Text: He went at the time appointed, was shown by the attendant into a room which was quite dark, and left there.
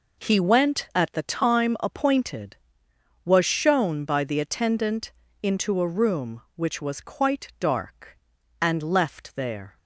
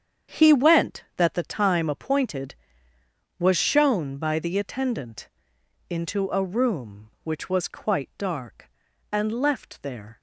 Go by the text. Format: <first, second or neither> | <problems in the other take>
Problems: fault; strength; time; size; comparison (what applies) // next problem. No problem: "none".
first | starts louder than the rest; strong; until 1.4 s; 8 dB // says "that" for "at"; at 1.1 s // pauses between "attendant" and "into"; noticeable; at 5.2 s; 0.62 s long; slight in the first